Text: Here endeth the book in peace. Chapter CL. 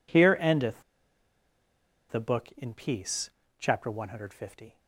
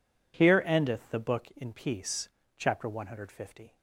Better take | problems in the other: second | pauses between "endeth" and "the"; strong; at 0.8 s; 1.2 s long

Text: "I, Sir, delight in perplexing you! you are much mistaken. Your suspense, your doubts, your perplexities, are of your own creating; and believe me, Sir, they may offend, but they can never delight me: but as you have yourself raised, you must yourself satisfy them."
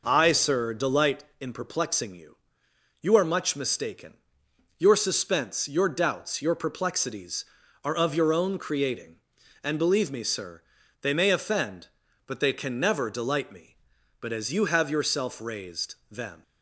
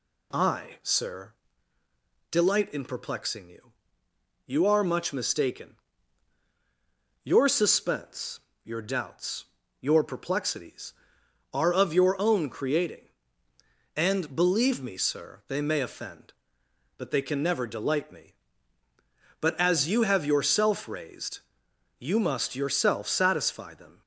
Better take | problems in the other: second | skips "you must yourself satisfy"; at 16.0 s

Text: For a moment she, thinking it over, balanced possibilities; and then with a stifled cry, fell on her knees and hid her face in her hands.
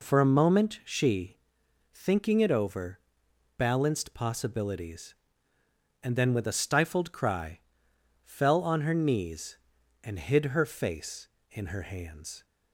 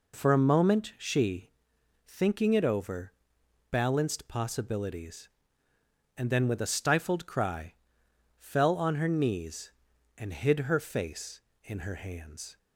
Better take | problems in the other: neither | none

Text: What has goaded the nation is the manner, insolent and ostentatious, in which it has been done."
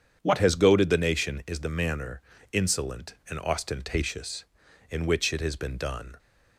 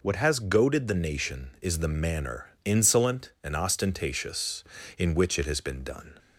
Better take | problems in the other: neither | none

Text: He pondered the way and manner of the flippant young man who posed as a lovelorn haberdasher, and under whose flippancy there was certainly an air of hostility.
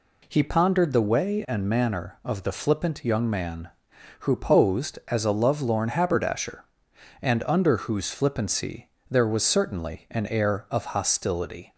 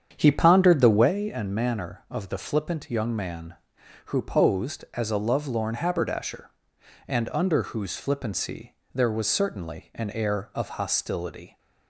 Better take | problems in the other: first | starts louder than the rest; strong; until 1.2 s; 8 dB // pauses between "flippancy" and "there"; slight; at 8.7 s; 0.20 s long; slight in the first

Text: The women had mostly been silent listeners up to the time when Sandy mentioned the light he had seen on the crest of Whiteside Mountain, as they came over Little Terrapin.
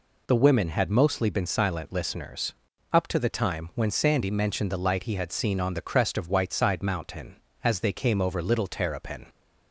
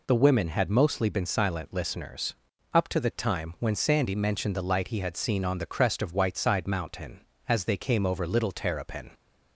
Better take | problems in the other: neither | pauses between "listeners" and "up"; the same in both

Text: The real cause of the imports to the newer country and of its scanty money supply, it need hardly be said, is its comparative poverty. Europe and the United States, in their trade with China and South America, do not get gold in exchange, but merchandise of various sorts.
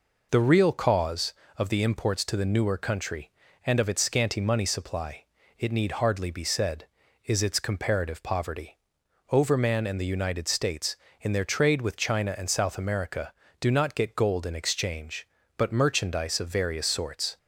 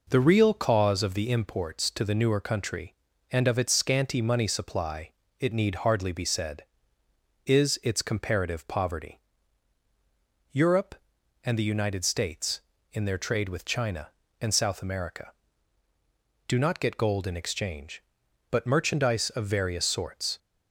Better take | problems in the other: second | says "Overman" for "Europe"; at 9.3 s

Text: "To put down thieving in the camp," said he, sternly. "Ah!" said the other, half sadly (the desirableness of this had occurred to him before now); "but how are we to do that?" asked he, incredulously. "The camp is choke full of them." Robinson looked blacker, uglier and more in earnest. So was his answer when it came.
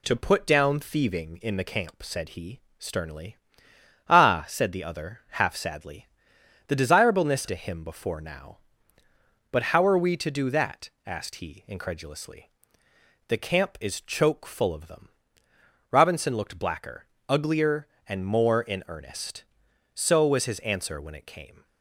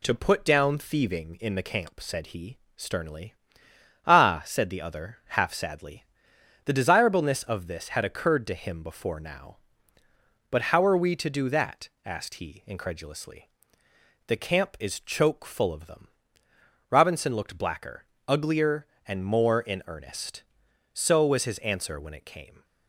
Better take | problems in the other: second | skips "of this had occurred"; at 7.4 s

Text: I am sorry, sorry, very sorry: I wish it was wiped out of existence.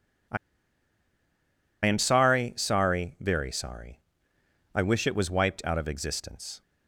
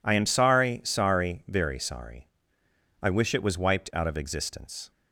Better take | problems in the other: second | pauses between "I" and "am"; strong; at 0.3 s; 1.4 s long

